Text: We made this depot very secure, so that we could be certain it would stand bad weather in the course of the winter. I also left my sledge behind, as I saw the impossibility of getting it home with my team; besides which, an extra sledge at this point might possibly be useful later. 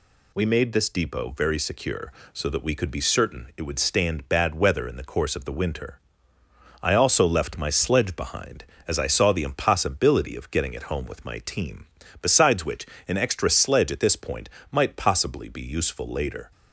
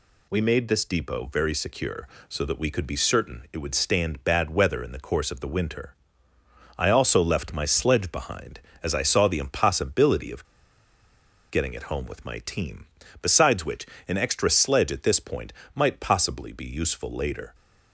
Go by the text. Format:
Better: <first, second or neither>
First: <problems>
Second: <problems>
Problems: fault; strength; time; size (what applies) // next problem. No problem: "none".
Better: first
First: pauses between "point" and "might"; slight; at 14.5 s; 0.20 s long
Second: pauses between "of" and "getting"; at 10.4 s; 1.0 s long // pauses between "point" and "might"; slight; at 15.5 s; 0.20 s long